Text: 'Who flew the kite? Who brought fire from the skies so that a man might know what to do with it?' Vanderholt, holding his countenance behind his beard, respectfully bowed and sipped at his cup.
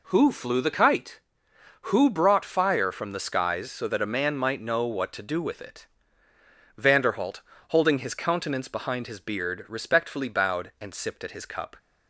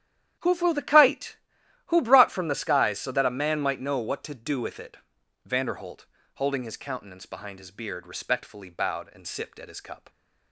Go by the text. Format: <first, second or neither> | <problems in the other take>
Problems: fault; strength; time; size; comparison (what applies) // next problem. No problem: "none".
first | starts louder than the rest; strong; until 1.9 s; 10.5 dB // skips "fire"; at 2.2 s